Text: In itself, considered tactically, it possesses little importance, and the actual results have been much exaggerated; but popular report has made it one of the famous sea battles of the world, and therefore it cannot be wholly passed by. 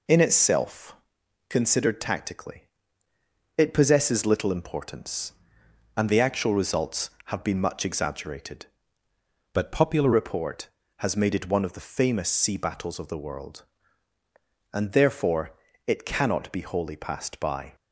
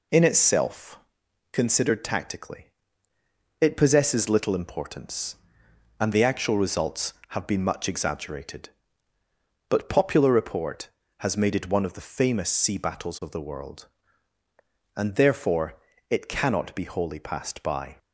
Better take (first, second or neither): second